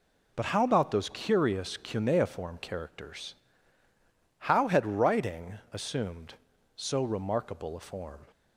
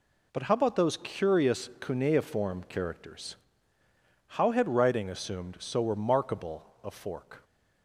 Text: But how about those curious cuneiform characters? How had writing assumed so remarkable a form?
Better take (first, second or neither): first